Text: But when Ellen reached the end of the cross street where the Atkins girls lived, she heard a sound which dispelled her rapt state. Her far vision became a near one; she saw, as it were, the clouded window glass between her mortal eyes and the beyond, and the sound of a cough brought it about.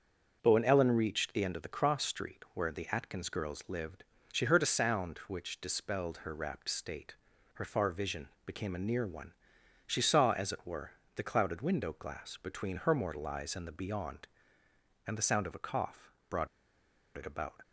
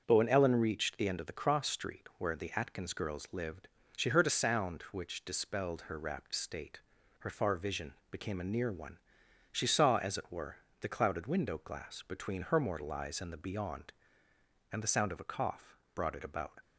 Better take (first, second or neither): second